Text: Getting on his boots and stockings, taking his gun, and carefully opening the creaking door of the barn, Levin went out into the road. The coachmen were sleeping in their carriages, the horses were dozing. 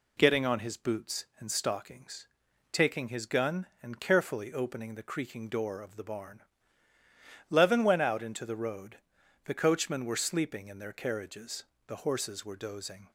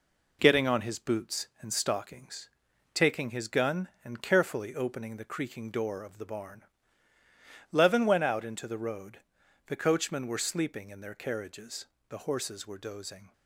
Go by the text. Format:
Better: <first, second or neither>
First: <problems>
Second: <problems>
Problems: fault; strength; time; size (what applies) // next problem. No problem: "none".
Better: first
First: none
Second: gets quieter; noticeable; throughout; 5 dB